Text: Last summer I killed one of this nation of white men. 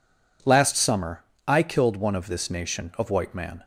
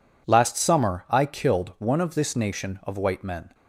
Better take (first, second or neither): second